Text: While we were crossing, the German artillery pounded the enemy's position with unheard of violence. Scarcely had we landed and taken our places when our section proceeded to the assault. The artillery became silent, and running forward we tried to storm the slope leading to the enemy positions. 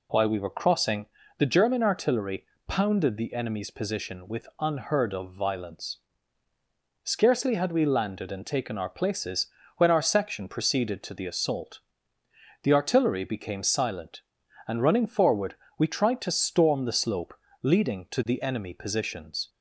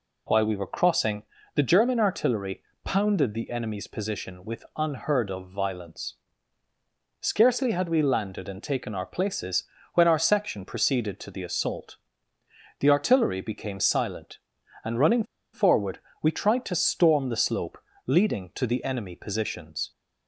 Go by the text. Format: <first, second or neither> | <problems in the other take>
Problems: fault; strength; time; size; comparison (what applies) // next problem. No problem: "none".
first | pauses between "artillery" and "pounded"; slight; at 2.6 s; 0.22 s long; slight in the first // pauses between "places" and "when"; slight; at 9.6 s; 0.30 s long; slight in the first // pauses between "running" and "forward"; slight; at 15.2 s; 0.29 s long // pauses between "forward" and "we"; slight; at 15.9 s; 0.24 s long; slight in the first // pauses between "slope" and "leading"; slight; at 17.7 s; 0.30 s long; slight in the first